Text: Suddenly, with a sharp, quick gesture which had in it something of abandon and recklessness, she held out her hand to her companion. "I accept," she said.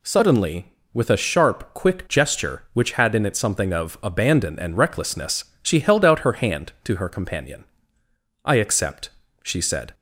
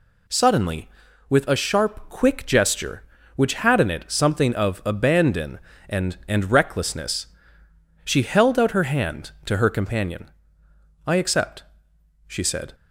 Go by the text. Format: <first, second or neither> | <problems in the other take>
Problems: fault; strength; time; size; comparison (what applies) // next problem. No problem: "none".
first | says "and" twice; at 6.2 s